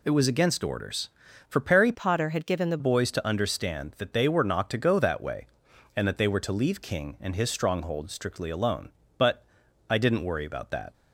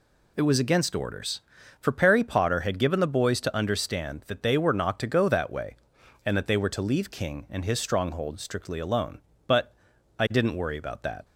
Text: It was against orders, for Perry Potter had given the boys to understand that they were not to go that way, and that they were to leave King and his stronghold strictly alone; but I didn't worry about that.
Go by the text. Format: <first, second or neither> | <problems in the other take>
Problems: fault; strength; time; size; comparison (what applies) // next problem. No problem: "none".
second | changes voice from "Potter" to "the"; from 1.9 to 2.7 s; 0.8 s long // pauses between "but" and "I"; noticeable; at 9.4 s; 0.46 s long; noticeable in the second